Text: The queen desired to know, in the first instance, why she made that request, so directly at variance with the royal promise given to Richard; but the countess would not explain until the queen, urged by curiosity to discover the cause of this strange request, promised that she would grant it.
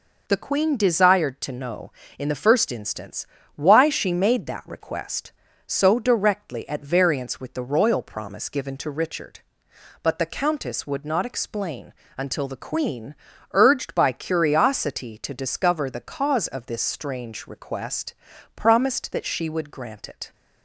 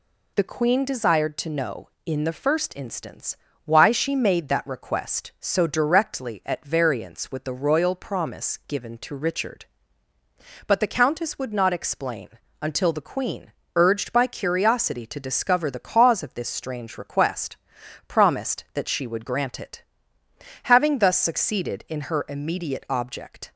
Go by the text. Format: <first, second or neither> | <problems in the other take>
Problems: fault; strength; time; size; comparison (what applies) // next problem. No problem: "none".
first | pauses between "explain" and "until"; slight; at 12.3 s; 0.30 s long; slight in the first // goes on to say "Having thus succeeded in her immediate object"; strong; from 20.6 s on; 2.8 s long